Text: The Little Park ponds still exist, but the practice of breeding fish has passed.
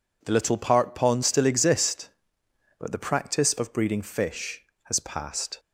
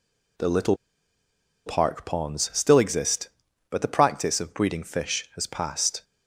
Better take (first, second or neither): first